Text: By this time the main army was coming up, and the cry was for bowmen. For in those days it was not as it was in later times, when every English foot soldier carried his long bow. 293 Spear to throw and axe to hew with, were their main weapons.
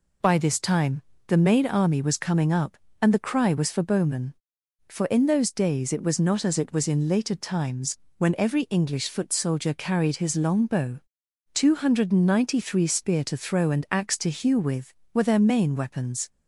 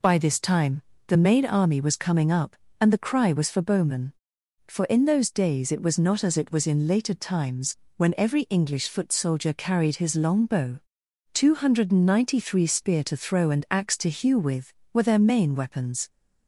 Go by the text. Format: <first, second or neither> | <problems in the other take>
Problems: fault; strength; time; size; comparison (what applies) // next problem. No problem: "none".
neither | pauses between "time" and "the"; slight; the same in both